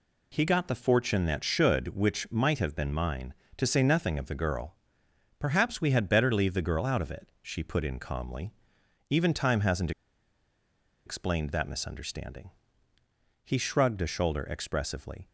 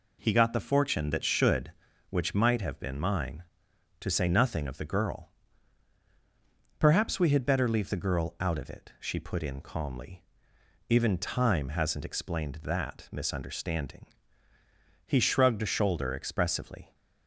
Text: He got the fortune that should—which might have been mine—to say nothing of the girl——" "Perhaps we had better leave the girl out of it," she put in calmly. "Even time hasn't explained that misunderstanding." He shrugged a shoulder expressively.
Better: second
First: pauses between "hasn't" and "explained"; at 9.9 s; 1.1 s long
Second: none

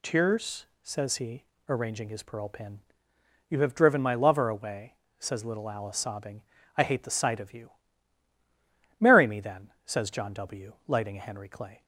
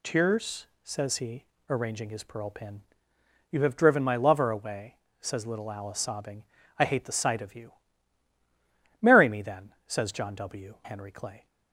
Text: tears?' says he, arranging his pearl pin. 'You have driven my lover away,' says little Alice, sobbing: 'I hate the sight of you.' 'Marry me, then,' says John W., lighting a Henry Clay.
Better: first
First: none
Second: skips "lighting a"; at 10.7 s

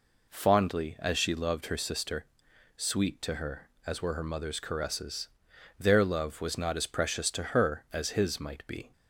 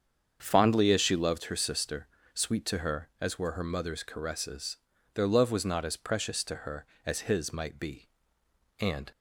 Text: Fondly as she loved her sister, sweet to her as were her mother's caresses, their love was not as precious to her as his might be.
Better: first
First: none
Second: starts louder than the rest; strong; until 1.4 s; 7.5 dB // goes on to say "And"; slight; from 8.7 s on; 0.32 s long

